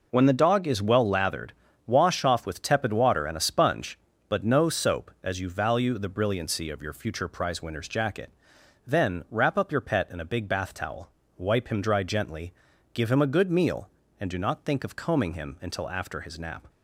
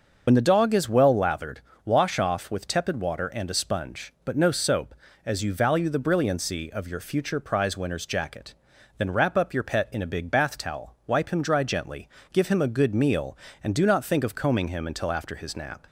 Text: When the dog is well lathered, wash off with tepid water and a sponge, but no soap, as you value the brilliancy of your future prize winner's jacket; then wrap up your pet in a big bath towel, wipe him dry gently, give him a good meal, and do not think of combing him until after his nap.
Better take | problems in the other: first | loses the start of "When"; at 0.2 s; 55 ms // starts louder than the rest; noticeable; until 1.2 s; 6 dB

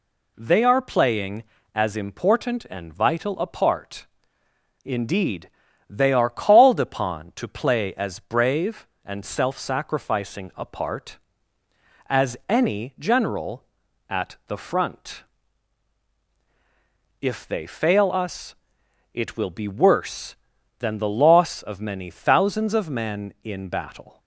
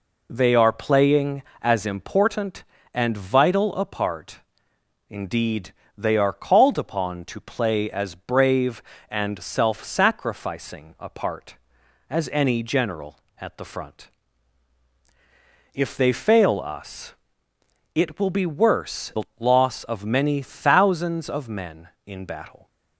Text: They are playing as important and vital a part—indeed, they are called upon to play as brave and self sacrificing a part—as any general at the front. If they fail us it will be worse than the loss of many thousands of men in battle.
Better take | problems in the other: first | pauses between "us" and "it"; noticeable; at 17.1 s; 0.80 s long; noticeable in the first // skips "than"; at 19.1 s // pauses between "the" and "loss"; slight; at 19.2 s; 0.16 s long

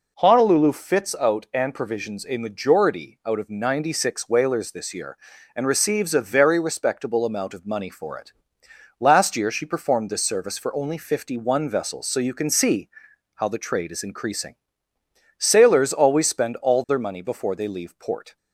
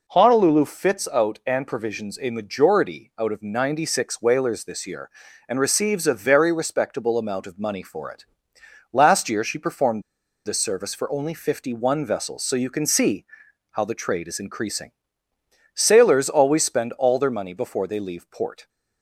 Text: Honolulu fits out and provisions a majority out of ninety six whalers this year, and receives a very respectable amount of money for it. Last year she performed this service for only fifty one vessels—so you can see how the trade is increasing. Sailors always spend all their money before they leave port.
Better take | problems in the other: first | pauses between "performed" and "this"; at 10.0 s; 0.44 s long // pauses between "see" and "how"; noticeable; at 13.2 s; 0.48 s long; noticeable in the first

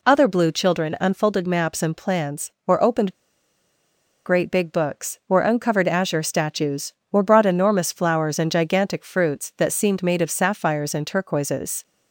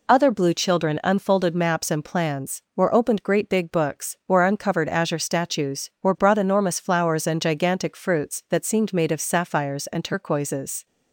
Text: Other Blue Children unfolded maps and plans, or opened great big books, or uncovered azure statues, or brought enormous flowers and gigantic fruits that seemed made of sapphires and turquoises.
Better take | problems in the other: second | pauses between "opened" and "great"; at 3.1 s; 1.1 s long

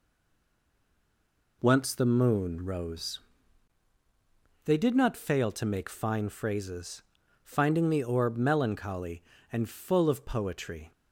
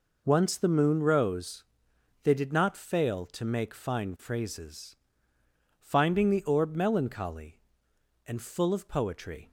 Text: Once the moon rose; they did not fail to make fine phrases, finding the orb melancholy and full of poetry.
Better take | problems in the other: second | stays silent before the first word; noticeable; until 1.6 s; 1.6 s long

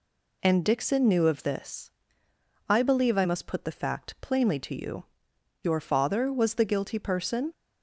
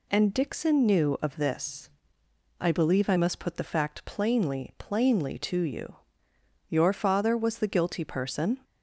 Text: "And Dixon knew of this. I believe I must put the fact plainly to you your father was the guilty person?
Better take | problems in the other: first | says "plainly" twice; at 4.7 s // pauses between "you" and "your"; noticeable; at 5.9 s; 0.72 s long; noticeable in the first

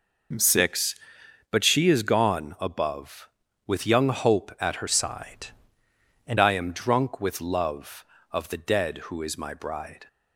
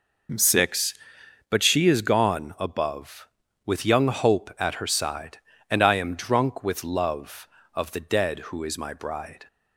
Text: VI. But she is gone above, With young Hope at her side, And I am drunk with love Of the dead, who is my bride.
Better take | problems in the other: second | changes voice from "side" to "And"; from 4.8 to 6.3 s; 1.5 s long

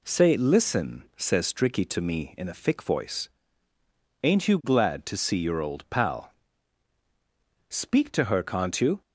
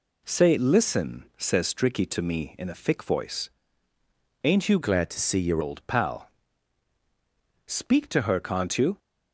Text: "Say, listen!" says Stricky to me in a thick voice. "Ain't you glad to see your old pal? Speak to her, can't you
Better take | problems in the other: first | changes voice from "glad" to "your"; from 4.8 to 5.6 s; 0.8 s long

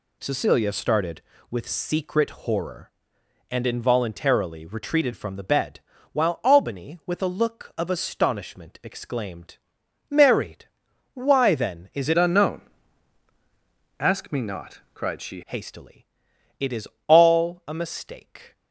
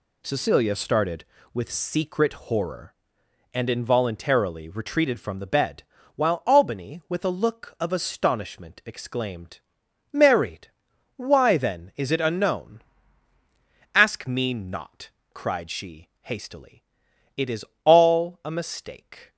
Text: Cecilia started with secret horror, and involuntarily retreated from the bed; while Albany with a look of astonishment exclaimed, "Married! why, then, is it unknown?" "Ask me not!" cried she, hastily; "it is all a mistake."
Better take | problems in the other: second | changes voice from "unknown" to "she"; from 12.1 to 15.4 s; 3.3 s long // pauses between "is" and "all"; slight; at 16.8 s; 0.22 s long; slight in the second

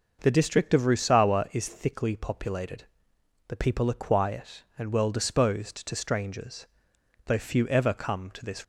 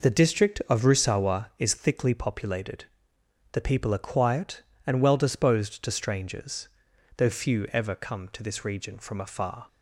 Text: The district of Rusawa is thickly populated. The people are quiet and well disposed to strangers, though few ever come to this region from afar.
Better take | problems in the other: second | starts louder than the rest; noticeable; until 1.2 s; 6 dB // stops before "region from afar"; at 8.6 s

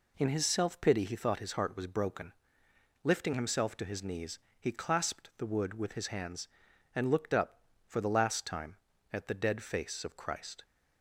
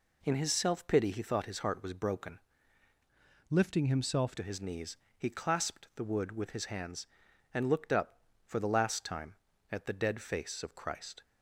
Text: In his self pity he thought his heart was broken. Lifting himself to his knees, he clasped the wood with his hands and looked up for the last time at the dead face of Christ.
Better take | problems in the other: first | changes voice from "Lifting" to "himself"; from 3.4 to 4.3 s; 0.9 s long

